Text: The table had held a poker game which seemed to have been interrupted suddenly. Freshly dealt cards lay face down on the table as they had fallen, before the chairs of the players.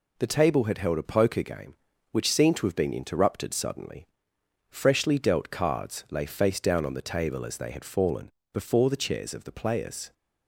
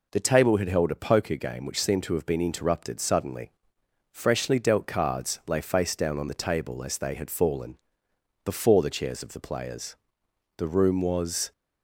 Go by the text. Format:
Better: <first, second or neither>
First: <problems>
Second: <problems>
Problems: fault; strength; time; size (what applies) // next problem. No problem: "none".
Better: first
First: none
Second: goes on to say "The room was"; noticeable; from 10.5 s on; 0.94 s long